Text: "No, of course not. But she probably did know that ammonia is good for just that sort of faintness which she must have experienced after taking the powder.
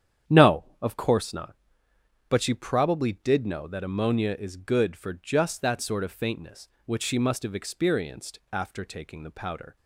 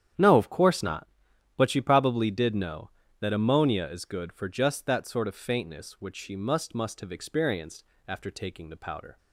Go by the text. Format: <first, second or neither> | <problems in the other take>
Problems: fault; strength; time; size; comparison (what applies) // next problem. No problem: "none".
first | starts louder than the rest; strong; until 1.6 s; 10 dB; strong in the first // says "must" twice; at 6.7 s // pauses between "experienced" and "after"; slight; at 7.8 s; 0.24 s long